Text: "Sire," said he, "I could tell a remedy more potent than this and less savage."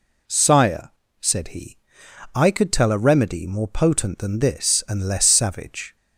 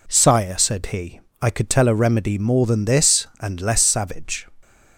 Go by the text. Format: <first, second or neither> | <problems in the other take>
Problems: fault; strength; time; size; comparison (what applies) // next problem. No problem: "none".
first | skips "potent"; at 2.6 s